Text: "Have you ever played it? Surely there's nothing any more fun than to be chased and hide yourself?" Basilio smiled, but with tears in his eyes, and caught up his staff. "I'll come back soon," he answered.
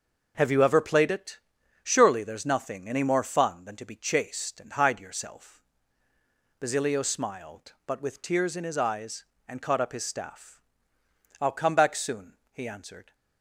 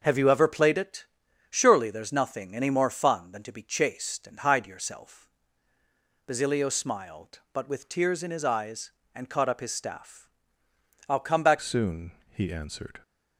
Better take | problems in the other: first | changes voice at "soon"; from 11.5 s on; 1.5 s long

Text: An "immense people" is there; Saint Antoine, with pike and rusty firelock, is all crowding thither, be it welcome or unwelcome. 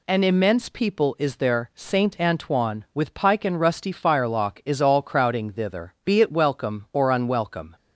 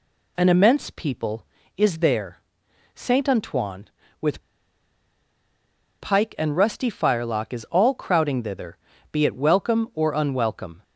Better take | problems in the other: first | pauses between "with" and "pike"; strong; at 4.4 s; 1.5 s long

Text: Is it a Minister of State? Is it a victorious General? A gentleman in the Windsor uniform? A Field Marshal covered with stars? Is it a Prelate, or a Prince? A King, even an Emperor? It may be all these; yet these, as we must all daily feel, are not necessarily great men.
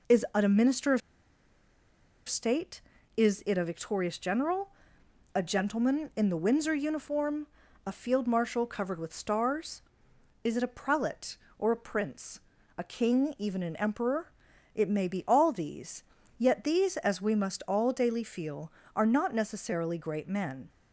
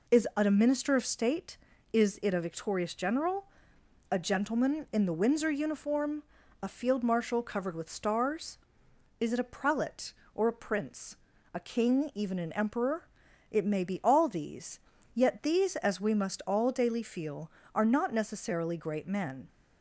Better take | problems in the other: second | pauses between "of" and "State"; strong; at 1.0 s; 1.2 s long

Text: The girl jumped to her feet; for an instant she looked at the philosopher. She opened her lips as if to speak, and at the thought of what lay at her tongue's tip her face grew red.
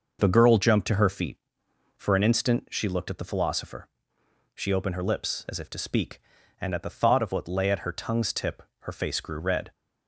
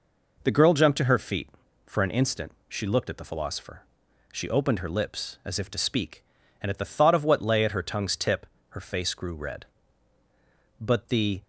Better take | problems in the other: first | pauses between "instant" and "she"; slight; at 2.5 s; 0.16 s long // pauses between "tip" and "her"; slight; at 8.4 s; 0.26 s long; slight in the first // goes on to say "But the"; noticeable; from 10.8 s on; 0.62 s long

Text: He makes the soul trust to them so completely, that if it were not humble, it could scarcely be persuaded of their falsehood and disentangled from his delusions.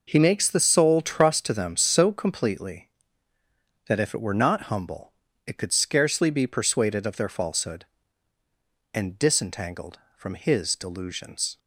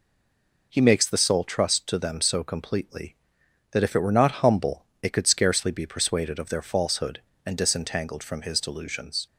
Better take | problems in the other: first | stays silent before the first word; slight; until 0.7 s; 0.7 s long

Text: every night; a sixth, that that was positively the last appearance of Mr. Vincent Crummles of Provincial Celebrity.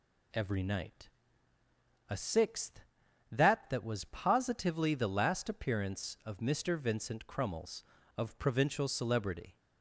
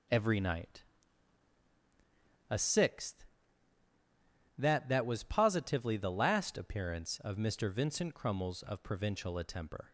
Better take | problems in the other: first | says "Attemper" for "Celebrity"; at 9.3 s

